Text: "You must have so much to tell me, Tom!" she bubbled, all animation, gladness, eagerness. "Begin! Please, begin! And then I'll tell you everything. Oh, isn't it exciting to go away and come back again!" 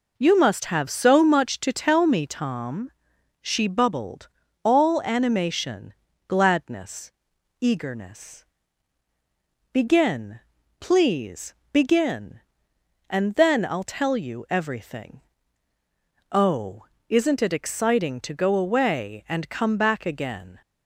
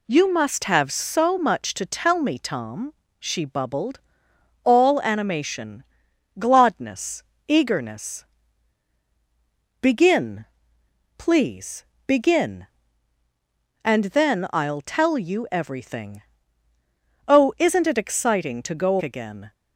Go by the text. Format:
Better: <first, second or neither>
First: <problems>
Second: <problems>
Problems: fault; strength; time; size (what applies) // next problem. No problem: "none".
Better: first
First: none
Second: skips "away and come back"; at 19.0 s